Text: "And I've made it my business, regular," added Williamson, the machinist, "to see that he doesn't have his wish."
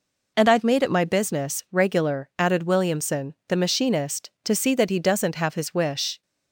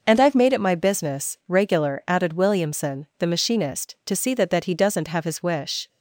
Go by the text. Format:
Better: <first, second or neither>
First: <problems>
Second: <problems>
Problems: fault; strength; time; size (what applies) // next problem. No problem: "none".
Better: first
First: none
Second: says "that" twice; at 4.4 s